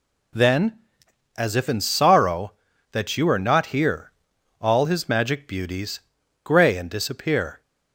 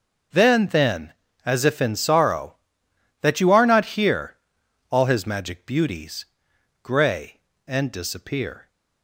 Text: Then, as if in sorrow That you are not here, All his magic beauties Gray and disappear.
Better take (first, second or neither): first